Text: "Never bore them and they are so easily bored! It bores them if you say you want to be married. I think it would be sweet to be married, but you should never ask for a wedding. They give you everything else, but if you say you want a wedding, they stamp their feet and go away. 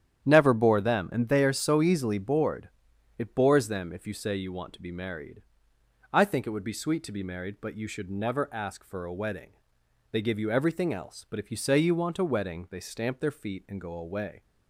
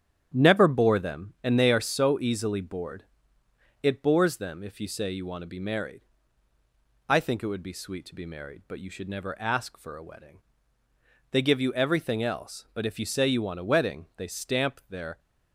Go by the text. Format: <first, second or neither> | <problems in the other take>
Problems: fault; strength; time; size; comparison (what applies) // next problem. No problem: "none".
first | starts louder than the rest; strong; until 1.3 s; 9.5 dB; strong in the first // stops before "feet and go away"; at 15.1 s